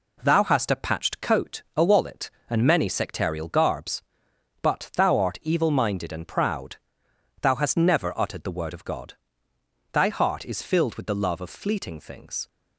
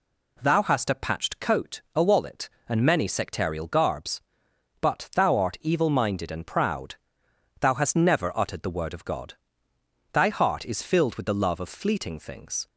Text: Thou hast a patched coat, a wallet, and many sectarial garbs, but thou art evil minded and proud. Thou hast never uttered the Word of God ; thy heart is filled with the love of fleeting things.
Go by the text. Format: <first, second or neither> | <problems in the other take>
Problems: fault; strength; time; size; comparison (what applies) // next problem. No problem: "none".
second | gets quieter; noticeable; throughout; 4.5 dB